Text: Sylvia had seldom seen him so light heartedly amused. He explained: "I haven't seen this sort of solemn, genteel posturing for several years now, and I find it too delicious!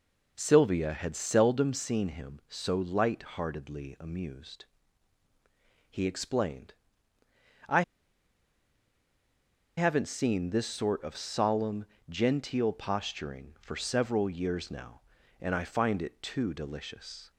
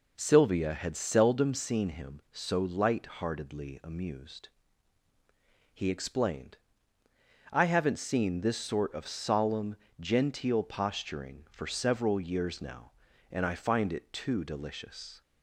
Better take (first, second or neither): second